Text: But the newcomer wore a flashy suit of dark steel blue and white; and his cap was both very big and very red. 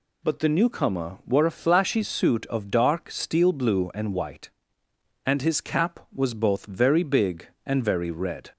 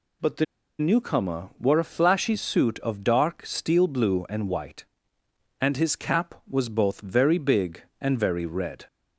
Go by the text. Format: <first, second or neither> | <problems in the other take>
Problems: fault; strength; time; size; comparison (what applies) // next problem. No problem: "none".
first | pauses between "the" and "newcomer"; slight; at 0.4 s; 0.34 s long